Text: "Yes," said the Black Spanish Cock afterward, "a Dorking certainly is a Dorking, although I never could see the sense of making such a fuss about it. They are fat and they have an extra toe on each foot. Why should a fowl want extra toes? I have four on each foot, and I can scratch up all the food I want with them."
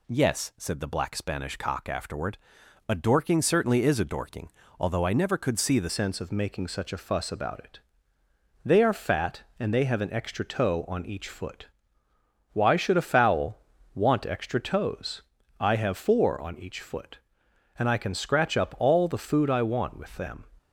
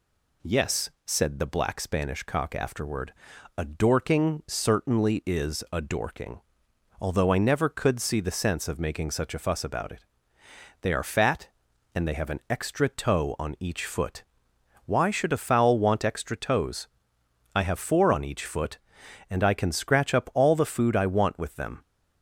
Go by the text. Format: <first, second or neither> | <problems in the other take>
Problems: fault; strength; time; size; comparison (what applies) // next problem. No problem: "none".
second | changes voice at "sense"; from 5.8 s on; 14.6 s long // pauses between "fowl" and "want"; slight; at 13.5 s; 0.36 s long